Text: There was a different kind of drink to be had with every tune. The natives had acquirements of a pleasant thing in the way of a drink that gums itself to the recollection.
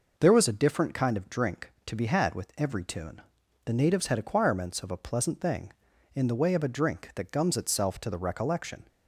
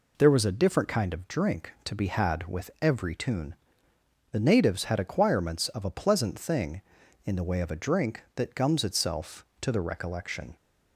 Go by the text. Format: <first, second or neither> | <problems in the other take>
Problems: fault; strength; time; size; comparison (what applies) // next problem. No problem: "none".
neither | none